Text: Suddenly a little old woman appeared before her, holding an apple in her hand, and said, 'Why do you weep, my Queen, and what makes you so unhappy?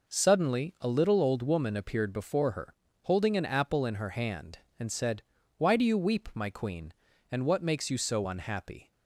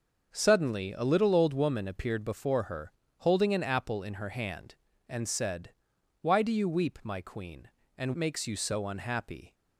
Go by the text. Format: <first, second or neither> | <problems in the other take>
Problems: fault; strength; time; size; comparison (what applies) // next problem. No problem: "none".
first | starts louder than the rest; until 1.3 s; 6 dB // skips "what"; at 8.1 s